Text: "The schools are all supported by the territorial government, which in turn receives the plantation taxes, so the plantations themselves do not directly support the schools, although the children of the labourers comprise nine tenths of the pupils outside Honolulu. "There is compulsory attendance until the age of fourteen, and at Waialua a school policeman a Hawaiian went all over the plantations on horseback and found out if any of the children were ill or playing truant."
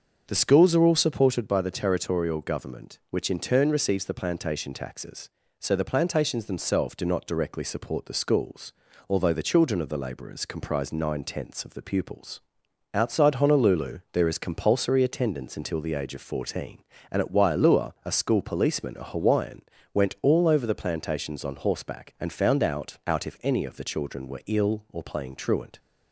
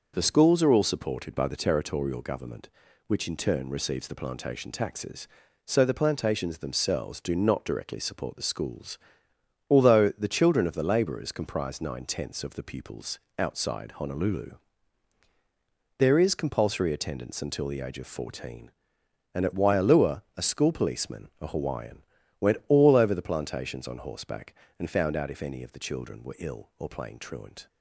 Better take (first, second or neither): second